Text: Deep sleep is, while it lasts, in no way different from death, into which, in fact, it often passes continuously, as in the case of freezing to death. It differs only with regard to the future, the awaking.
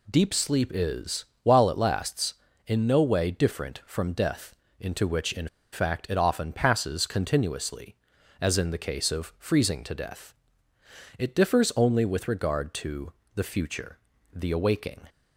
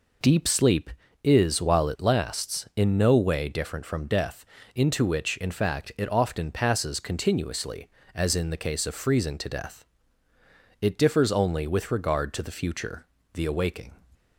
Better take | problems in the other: second | pauses between "in" and "fact"; slight; at 5.4 s; 0.25 s long // pauses between "to" and "the"; slight; at 13.1 s; 0.22 s long

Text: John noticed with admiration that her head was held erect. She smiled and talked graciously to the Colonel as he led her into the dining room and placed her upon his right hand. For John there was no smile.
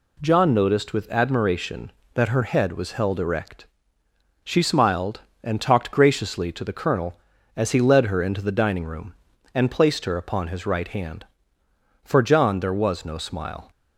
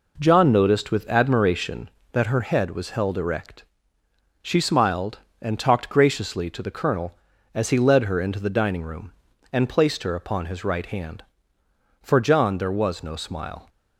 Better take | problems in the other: first | starts louder than the rest; noticeable; until 1.9 s; 4.5 dB

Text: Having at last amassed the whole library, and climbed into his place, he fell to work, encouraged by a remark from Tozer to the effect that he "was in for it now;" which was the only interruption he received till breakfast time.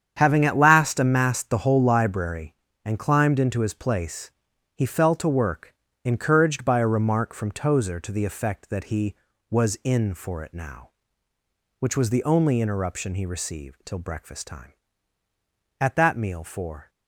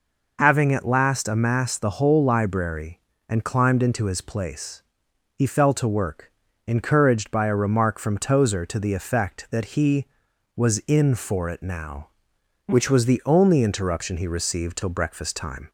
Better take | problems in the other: second | starts louder than the rest; strong; until 1.1 s; 8.5 dB // goes on to say "At that meal for"; noticeable; from 15.7 s on; 1.1 s long

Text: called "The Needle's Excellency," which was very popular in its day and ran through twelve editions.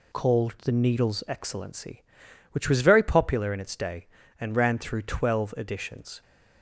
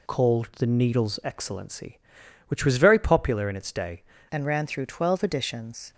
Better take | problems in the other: first | changes voice at "and"; from 4.2 s on; 1.7 s long

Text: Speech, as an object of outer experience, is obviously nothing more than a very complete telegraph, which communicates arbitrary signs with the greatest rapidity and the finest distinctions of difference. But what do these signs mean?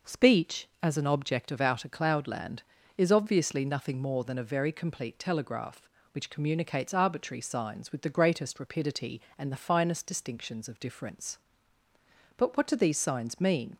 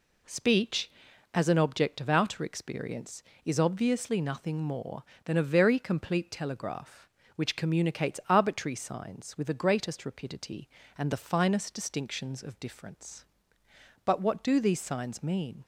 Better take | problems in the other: second | says "cloudland" for "experience"; at 1.8 s

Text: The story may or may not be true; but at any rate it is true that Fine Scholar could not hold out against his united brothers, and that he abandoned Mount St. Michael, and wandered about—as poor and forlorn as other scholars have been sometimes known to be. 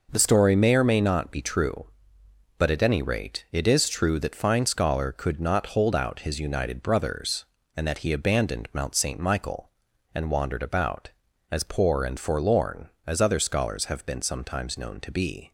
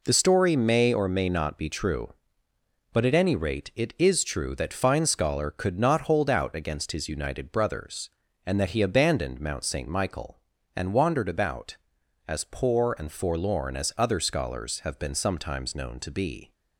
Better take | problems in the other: second | skips "against"; at 6.1 s

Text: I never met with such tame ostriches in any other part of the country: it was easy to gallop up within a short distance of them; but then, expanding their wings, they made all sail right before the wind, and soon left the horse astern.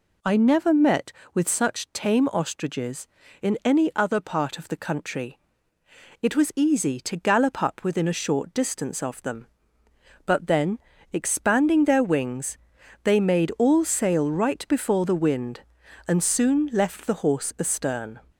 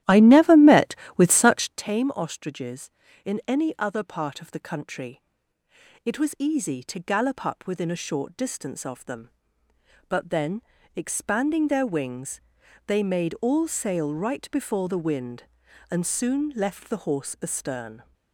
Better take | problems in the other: first | starts louder than the rest; strong; until 1.9 s; 13 dB

